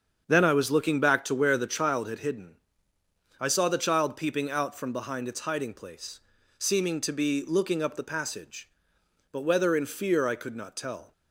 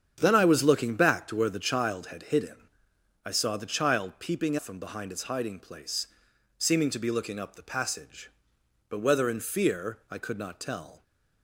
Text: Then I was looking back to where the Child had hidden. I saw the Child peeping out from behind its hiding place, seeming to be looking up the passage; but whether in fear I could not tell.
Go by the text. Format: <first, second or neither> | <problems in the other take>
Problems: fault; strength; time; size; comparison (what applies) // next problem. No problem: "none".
first | starts louder than the rest; strong; until 1.2 s; 8.5 dB; strong in the first // skips "out"; at 4.5 s